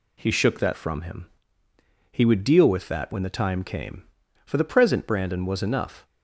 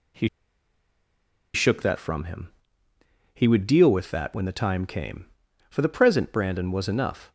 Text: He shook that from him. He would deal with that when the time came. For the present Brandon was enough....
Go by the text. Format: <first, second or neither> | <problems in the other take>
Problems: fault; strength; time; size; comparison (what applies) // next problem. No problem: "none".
first | pauses between "He" and "shook"; strong; at 0.2 s; 1.2 s long